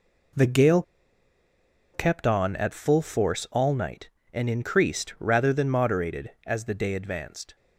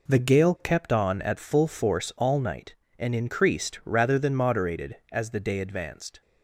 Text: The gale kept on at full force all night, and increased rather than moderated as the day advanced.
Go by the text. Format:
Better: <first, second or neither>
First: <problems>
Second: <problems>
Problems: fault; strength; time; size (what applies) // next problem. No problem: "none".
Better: second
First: pauses between "gale" and "kept"; at 0.8 s; 1.1 s long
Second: none